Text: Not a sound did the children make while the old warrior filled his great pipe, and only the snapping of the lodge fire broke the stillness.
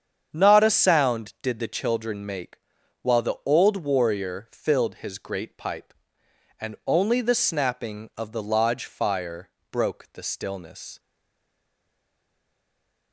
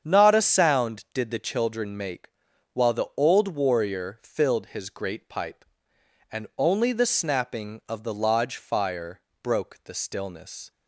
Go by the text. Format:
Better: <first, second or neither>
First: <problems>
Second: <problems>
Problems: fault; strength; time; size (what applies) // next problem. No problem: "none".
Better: second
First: starts louder than the rest; strong; until 1.3 s; 7.5 dB // pauses between "make" and "while"; at 2.5 s; 0.42 s long // pauses between "fire" and "broke"; slight; at 9.4 s; 0.22 s long // stays silent after the last word; from 10.9 s on; 2.2 s long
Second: starts louder than the rest; strong; until 1.0 s; 7.5 dB // pauses between "make" and "while"; at 2.3 s; 0.42 s long // pauses between "fire" and "broke"; slight; at 9.2 s; 0.22 s long